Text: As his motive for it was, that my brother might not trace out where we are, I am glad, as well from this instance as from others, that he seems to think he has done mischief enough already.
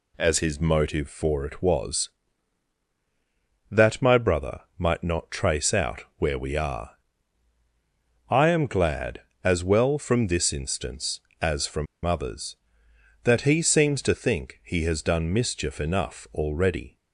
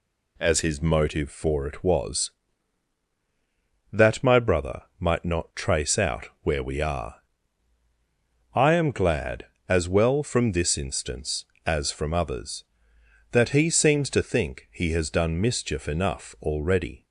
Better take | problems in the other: second | pauses between "brother" and "might"; slight; at 4.6 s; 0.16 s long; slight in the second // pauses between "from" and "others"; slight; at 11.8 s; 0.19 s long

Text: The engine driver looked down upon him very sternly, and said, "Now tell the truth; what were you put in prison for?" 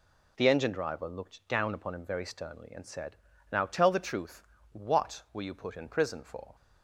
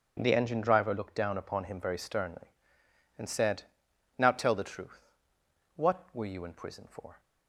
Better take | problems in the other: first | starts louder than the rest; until 1.2 s; 6.5 dB // skips "put"; at 6.4 s

